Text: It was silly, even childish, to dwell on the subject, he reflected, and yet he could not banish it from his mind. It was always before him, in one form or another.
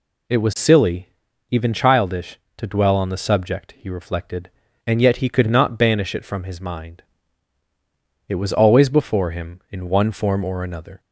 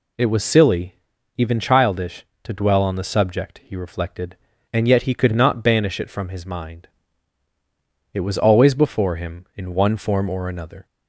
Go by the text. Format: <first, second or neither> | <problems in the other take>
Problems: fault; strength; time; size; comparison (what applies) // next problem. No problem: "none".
neither | none